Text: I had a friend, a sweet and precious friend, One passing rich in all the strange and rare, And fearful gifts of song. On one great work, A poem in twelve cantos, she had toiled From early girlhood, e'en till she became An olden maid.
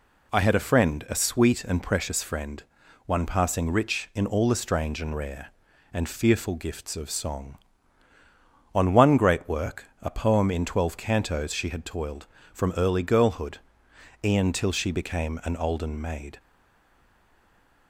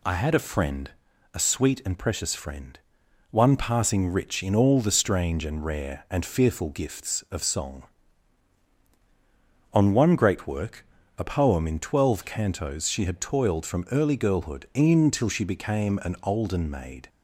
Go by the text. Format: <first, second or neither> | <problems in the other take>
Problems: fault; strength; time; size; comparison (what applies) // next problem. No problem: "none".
second | stays silent after the last word; noticeable; from 16.3 s on; 1.5 s long